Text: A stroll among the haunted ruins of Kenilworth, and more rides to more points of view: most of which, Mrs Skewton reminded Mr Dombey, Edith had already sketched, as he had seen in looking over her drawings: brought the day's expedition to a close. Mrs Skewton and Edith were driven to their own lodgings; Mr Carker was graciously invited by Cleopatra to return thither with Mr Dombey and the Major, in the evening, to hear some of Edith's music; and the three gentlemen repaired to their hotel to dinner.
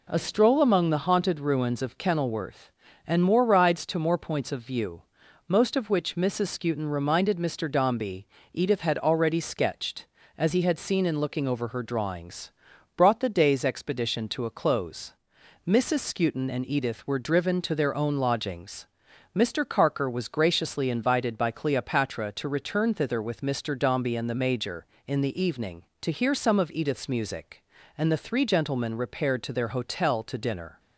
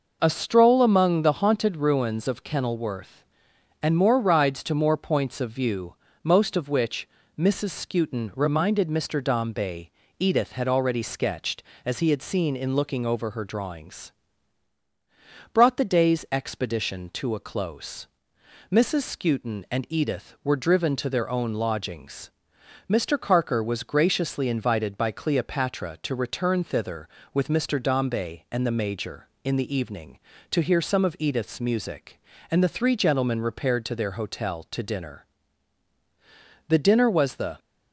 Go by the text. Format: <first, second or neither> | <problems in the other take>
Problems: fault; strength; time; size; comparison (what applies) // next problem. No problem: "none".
first | goes on to say "The dinner was the"; noticeable; from 36.6 s on; 0.90 s long